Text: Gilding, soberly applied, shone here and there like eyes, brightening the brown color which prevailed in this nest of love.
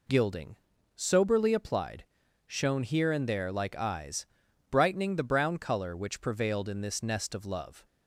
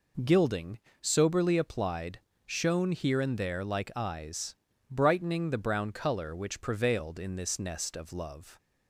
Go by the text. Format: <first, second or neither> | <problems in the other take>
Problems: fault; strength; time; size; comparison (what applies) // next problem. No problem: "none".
neither | none